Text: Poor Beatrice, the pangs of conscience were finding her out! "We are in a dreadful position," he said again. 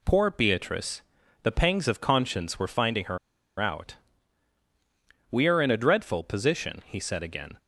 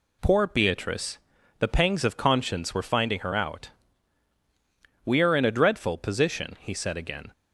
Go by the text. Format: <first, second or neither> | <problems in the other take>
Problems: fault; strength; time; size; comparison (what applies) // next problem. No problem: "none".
second | pauses between "her" and "out"; at 3.1 s; 0.41 s long